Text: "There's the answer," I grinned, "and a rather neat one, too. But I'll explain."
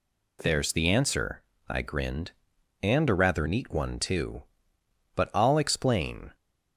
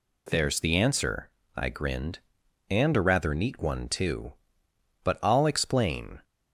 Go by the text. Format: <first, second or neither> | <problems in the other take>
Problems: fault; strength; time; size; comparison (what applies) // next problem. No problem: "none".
neither | none